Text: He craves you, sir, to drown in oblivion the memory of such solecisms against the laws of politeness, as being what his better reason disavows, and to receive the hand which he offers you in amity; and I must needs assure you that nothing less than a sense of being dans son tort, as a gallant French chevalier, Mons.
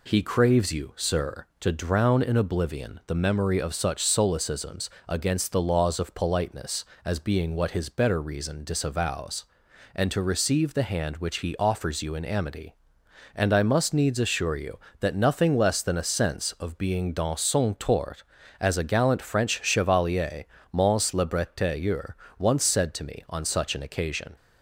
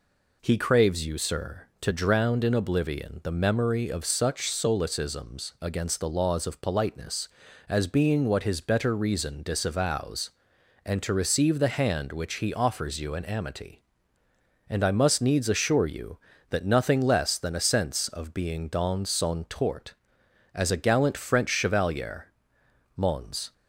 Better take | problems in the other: second | pauses between "solecisms" and "against"; slight; at 4.8 s; 0.20 s long // goes on to say "Le Bretailleur once said to me on such an occasion"; strong; from 21.1 s on; 3.2 s long

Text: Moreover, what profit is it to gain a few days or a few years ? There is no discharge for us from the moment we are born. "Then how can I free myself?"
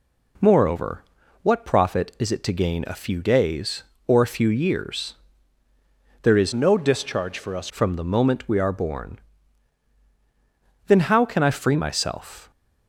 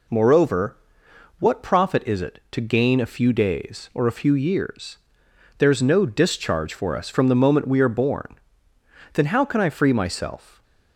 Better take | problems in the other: second | changes voice from "no" to "us"; from 6.5 to 7.6 s; 1.1 s long

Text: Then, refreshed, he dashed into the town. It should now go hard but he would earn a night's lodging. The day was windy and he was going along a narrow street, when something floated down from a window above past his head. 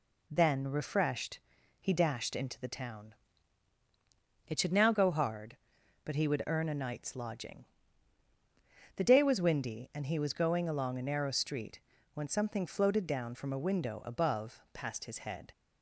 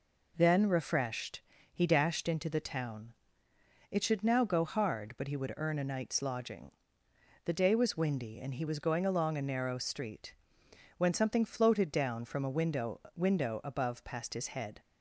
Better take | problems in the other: first | says "window" twice; at 13.1 s

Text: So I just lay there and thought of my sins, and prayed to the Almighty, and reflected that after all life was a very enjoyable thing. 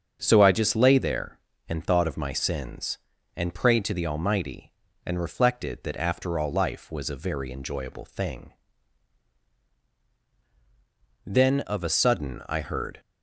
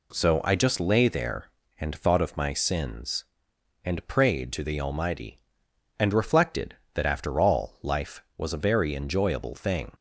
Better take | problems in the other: second | starts louder than the rest; strong; until 1.2 s; 7.5 dB // goes on to say "Then of a sudden I heard"; strong; from 11.2 s on; 1.7 s long

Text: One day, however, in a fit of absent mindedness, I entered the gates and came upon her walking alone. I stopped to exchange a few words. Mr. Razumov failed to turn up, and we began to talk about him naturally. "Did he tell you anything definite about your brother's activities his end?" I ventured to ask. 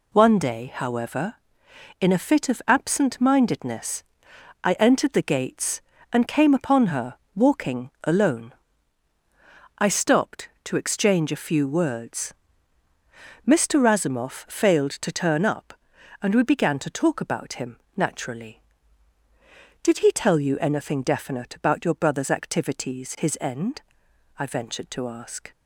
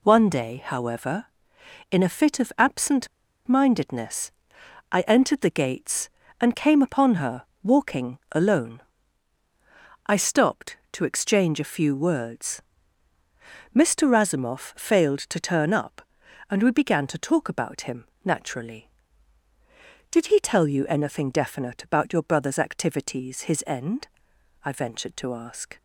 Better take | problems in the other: first | pauses between "absent" and "mindedness"; at 3.0 s; 0.39 s long // pauses between "her" and "walking"; slight; at 7.4 s; 0.20 s long; slight in the first // pauses between "him" and "naturally"; slight; at 18.0 s; 0.20 s long; slight in the first

